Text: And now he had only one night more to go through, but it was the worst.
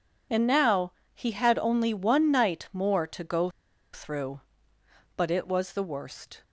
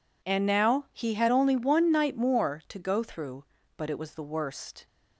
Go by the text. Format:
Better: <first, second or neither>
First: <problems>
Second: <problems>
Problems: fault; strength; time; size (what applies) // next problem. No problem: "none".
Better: second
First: pauses between "now" and "he"; slight; at 0.9 s; 0.20 s long // pauses between "go" and "through"; at 3.5 s; 0.42 s long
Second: none